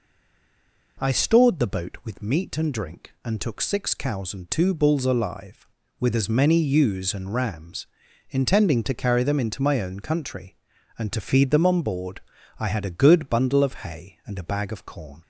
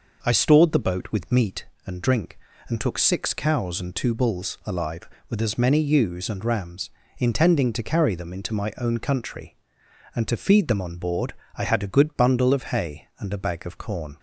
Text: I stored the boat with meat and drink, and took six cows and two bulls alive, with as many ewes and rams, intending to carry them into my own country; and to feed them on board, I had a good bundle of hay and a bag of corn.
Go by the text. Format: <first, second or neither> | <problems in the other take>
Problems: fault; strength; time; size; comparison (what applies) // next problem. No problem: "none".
second | stays silent before the first word; slight; until 0.9 s; 0.9 s long